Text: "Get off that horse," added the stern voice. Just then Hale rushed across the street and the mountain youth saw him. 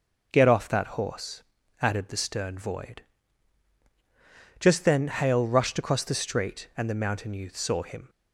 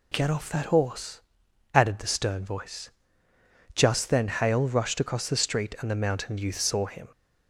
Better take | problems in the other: second | says "void" for "voice"; at 2.5 s

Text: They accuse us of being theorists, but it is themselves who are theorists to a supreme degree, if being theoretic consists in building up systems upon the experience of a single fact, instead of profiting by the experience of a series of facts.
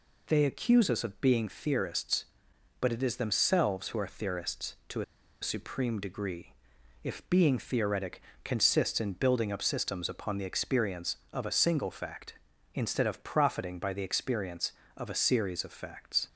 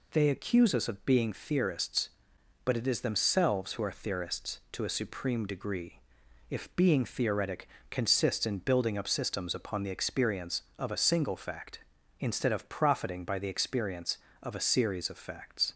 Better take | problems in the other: second | pauses between "to" and "a"; at 5.0 s; 0.38 s long // pauses between "theoretic" and "consists"; slight; at 8.2 s; 0.22 s long; slight in the second

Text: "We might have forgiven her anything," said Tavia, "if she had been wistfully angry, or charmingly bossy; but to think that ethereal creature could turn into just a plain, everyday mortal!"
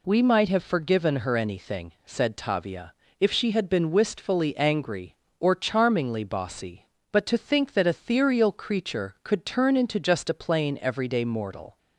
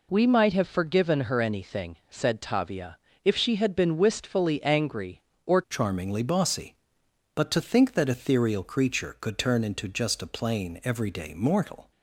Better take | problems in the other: first | changes voice at "charmingly"; from 5.6 s on; 6.3 s long

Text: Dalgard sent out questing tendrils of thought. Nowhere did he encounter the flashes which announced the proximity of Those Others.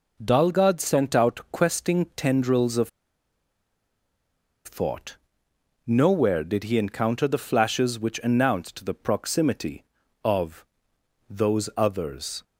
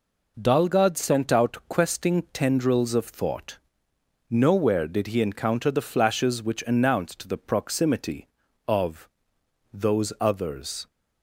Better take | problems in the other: second | pauses between "of" and "thought"; strong; at 2.8 s; 1.7 s long // pauses between "of" and "Those"; noticeable; at 10.6 s; 0.62 s long; noticeable in the second

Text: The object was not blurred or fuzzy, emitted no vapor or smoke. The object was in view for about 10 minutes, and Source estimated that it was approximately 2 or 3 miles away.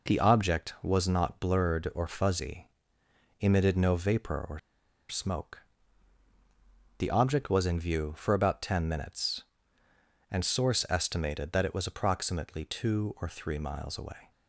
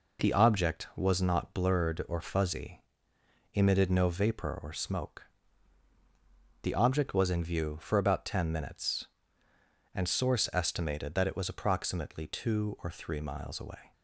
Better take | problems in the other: second | pauses between "or" and "smoke"; noticeable; at 4.5 s; 0.52 s long

